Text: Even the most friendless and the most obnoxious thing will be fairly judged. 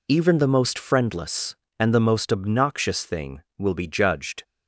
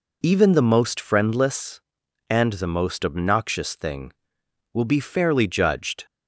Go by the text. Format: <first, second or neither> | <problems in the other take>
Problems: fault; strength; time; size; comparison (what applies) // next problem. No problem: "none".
second | skips "fairly"; at 3.8 s